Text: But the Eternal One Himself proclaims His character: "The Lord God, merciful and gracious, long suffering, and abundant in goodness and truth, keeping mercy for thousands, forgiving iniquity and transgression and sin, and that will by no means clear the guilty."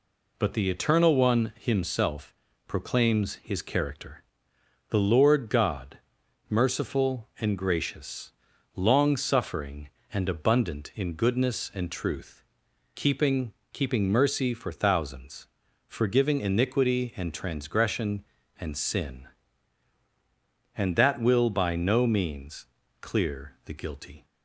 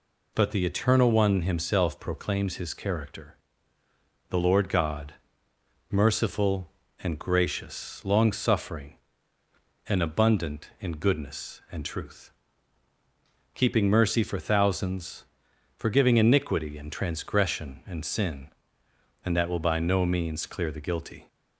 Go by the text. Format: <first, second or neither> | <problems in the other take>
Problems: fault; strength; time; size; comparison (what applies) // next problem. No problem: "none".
second | pauses between "Himself" and "proclaims"; slight; at 2.3 s; 0.32 s long // says "keeping" twice; at 13.7 s // pauses between "means" and "clear"; slight; at 22.6 s; 0.36 s long